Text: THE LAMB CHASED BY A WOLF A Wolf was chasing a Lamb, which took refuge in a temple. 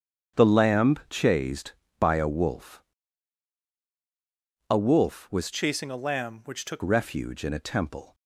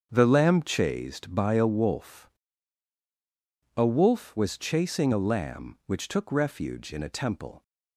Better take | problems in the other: second | starts louder than the rest; strong; until 1.5 s; 7.5 dB; strong in the second // pauses between "WOLF" and "A"; strong; at 2.8 s; 1.8 s long; strong in the second // changes voice from "chasing" to "took"; from 5.5 to 6.8 s; 1.3 s long

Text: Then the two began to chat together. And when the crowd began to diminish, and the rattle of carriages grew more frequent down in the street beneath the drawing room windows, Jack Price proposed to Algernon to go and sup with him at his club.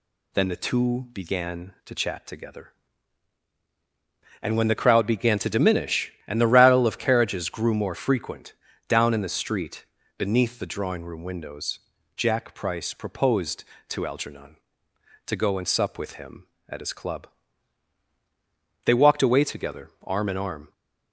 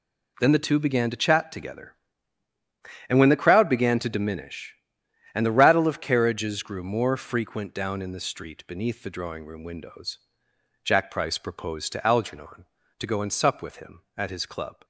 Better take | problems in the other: second | pauses between "frequent" and "down"; slight; at 8.5 s; 0.34 s long // pauses between "street" and "beneath"; slight; at 9.8 s; 0.34 s long // goes on to say "They walked away together arm in arm"; strong; from 18.8 s on; 1.8 s long

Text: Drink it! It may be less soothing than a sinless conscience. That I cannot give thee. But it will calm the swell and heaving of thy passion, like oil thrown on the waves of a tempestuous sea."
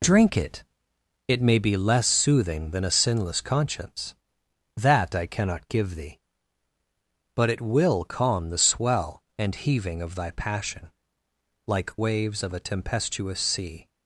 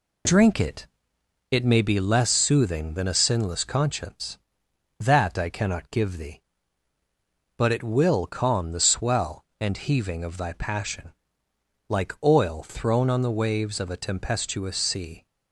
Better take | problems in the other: second | skips "oil thrown on the"; at 11.9 s

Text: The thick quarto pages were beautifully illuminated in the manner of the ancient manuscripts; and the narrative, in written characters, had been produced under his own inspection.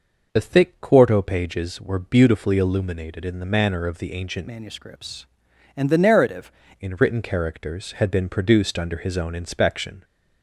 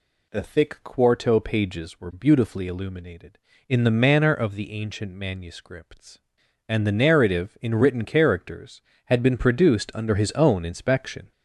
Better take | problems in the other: second | changes voice from "manuscripts" to "narrative"; from 4.4 to 6.4 s; 2.0 s long

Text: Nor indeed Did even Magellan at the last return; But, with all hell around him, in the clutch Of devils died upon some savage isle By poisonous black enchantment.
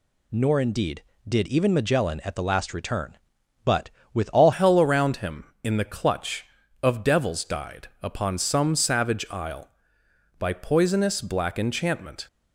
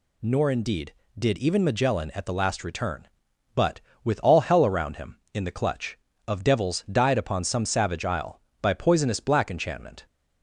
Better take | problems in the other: second | changes voice at "hell"; from 4.5 s on; 7.7 s long // pauses between "died" and "upon"; slight; at 7.8 s; 0.16 s long

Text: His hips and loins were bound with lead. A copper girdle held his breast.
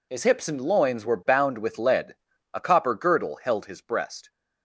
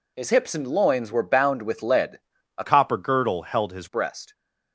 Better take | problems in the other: first | changes voice from "copper" to "his"; from 2.6 to 3.8 s; 1.2 s long

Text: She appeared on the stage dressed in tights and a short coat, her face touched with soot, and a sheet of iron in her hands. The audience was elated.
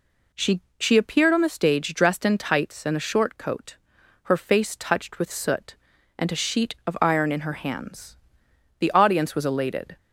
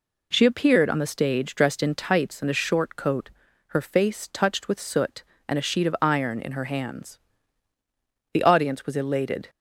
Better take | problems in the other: second | says "She" twice; at 0.7 s

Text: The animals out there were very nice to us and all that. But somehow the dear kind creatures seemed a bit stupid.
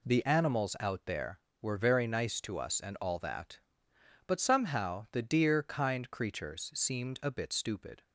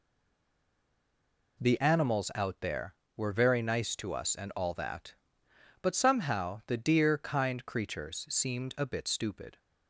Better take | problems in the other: first | stays silent before the first word; noticeable; until 1.5 s; 1.5 s long

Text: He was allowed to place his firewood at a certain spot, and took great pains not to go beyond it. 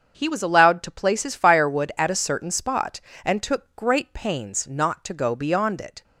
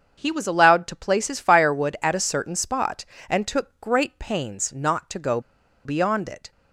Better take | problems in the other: first | starts louder than the rest; strong; until 1.1 s; 7 dB; strong in the first // pauses between "go" and "beyond"; at 5.4 s; 0.44 s long

